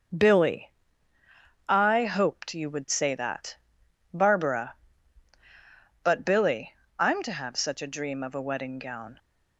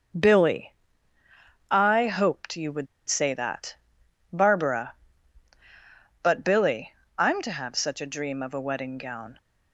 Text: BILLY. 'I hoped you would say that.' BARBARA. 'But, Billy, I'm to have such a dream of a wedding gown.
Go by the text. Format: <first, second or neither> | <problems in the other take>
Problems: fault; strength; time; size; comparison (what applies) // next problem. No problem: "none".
first | starts louder than the rest; until 2.1 s; 6 dB; also in the first // pauses between "would" and "say"; slight; at 2.8 s; 0.20 s long